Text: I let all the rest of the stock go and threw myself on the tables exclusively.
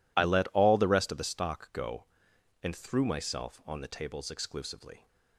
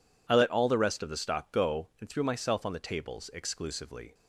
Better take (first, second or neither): neither